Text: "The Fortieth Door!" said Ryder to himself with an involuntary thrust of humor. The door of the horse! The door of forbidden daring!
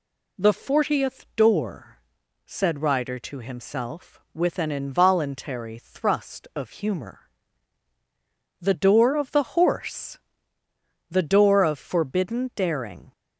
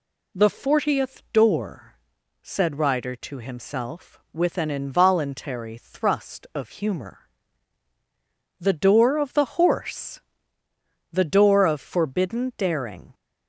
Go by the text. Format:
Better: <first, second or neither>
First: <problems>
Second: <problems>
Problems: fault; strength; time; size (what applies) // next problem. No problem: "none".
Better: neither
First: none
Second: none